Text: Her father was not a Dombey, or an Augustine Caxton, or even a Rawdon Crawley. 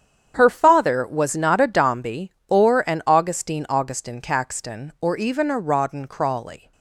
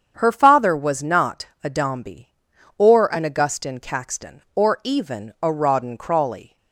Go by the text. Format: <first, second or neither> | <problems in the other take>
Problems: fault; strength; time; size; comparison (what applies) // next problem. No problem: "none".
second | starts louder than the rest; strong; until 1.3 s; 8.5 dB; strong in the second // says "Augustine" twice; at 3.6 s